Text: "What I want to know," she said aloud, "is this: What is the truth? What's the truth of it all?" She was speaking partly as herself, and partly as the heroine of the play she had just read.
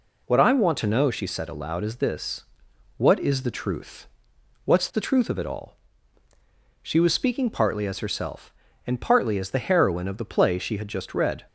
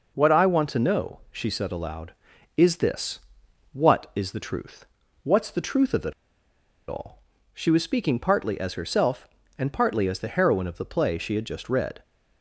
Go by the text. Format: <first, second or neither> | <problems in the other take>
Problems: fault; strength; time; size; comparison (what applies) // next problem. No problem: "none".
first | pauses between "it" and "all"; noticeable; at 6.1 s; 0.75 s long